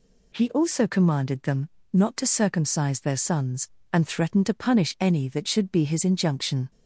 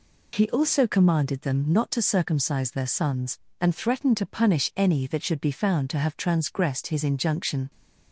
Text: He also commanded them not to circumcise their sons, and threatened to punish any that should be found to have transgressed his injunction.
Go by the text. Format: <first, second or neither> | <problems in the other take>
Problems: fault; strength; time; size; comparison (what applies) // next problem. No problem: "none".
second | pauses between "them" and "not"; slight; at 1.6 s; 0.24 s long // skips "found to have transgressed"; at 5.8 s